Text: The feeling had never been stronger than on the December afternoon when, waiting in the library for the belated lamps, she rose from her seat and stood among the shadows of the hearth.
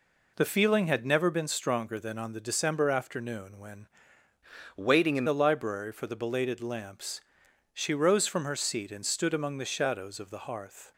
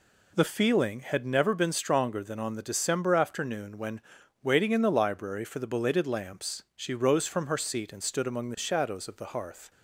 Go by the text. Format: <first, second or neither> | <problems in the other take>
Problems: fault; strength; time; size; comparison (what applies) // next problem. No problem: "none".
second | changes voice from "waiting" to "in"; from 4.7 to 5.2 s; 0.5 s long